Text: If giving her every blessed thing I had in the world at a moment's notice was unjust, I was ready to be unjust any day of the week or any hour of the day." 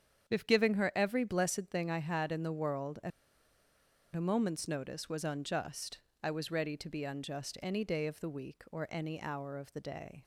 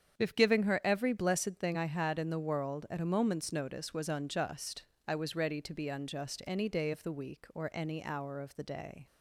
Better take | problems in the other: second | starts louder than the rest; strong; until 1.3 s; 8 dB; strong in the second // pauses between "at" and "a"; at 3.1 s; 1.0 s long

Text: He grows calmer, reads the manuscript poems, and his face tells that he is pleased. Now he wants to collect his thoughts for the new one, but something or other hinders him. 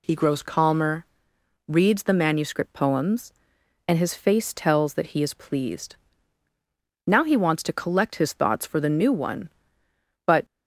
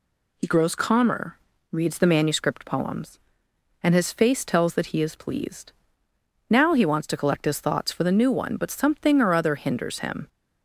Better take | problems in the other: second | stops before "something or other hinders him"; at 10.4 s

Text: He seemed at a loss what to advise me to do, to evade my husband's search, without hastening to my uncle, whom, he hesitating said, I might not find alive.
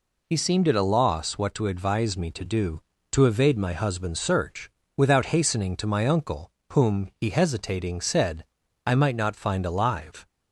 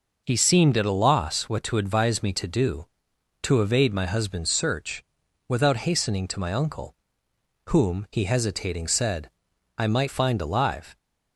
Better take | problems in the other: first | skips "not"; at 10.0 s

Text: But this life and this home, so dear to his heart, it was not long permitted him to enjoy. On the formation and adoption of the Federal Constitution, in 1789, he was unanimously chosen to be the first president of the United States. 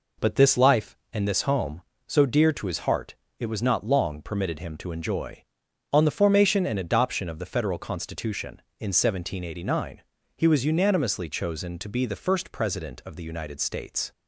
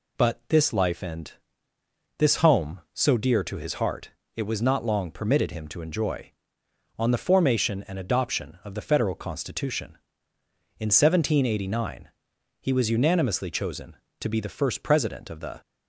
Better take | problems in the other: first | pauses between "and" and "this"; noticeable; at 1.3 s; 0.88 s long // stops before "United States"; at 15.6 s

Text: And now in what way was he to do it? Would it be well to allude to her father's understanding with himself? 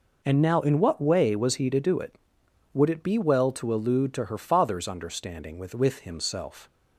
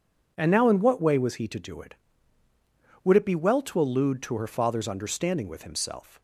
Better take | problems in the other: second | says "with" twice; at 5.7 s

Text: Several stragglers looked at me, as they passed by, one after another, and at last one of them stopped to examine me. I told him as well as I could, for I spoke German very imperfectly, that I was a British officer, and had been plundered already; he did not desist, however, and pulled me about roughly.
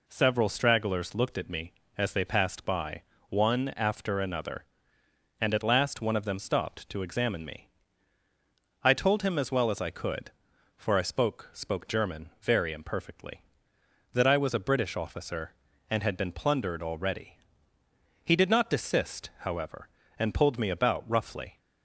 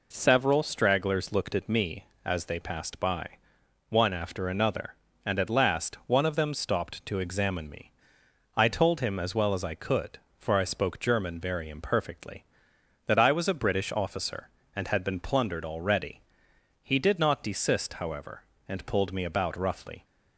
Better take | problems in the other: second | says "spoke" twice; at 11.5 s

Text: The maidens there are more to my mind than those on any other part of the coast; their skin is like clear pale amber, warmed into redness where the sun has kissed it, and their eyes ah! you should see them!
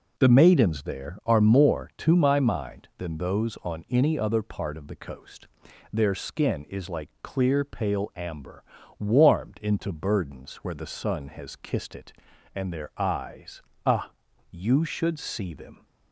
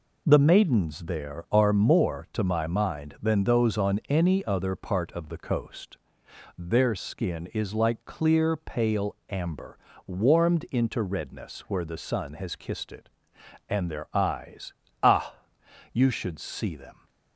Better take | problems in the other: second | says "burdens" for "redness"; at 9.9 s // pauses between "eyes" and "ah"; slight; at 13.6 s; 0.24 s long; slight in the second

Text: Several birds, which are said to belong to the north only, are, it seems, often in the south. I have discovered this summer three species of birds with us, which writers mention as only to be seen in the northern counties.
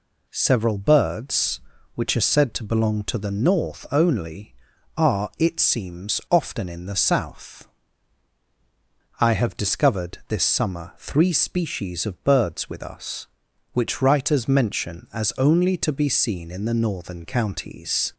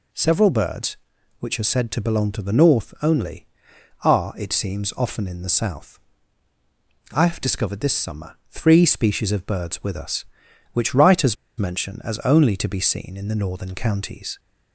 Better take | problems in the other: first | pauses between "writers" and "mention"; slight; at 11.3 s; 0.23 s long

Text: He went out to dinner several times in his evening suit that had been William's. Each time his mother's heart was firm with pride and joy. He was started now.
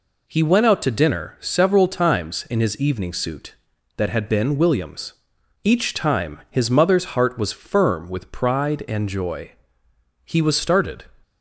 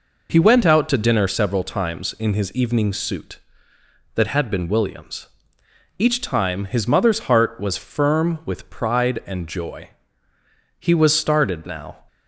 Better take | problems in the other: second | stops before "now"; at 11.2 s

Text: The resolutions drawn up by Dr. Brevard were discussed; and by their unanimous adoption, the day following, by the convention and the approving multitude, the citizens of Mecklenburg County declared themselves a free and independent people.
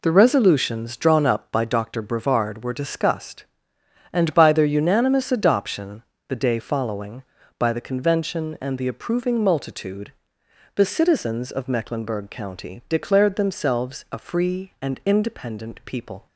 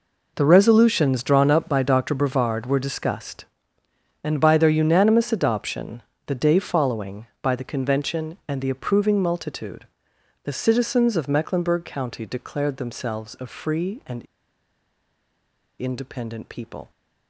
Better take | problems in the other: first | pauses between "and" and "independent"; strong; at 14.2 s; 1.5 s long

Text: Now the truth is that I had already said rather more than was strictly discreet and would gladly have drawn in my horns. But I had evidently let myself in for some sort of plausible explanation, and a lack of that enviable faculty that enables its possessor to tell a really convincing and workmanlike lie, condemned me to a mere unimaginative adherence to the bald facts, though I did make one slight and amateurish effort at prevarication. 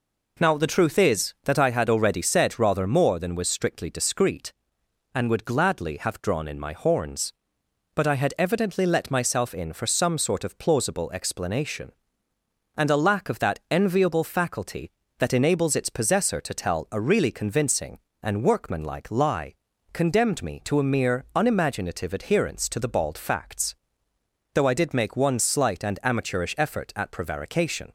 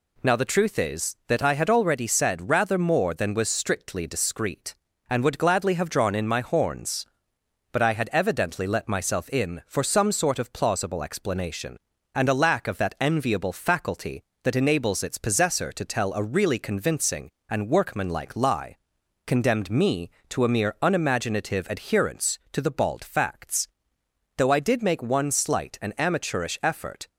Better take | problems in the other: first | stops before "at prevarication"; at 27.0 s

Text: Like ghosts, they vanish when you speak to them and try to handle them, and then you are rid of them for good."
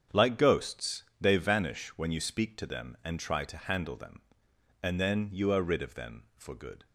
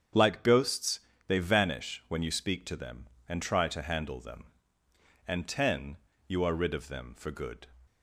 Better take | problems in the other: first | starts louder than the rest; strong; until 1.4 s; 8 dB; strong in the first // says "ten" for "then"; at 5.4 s

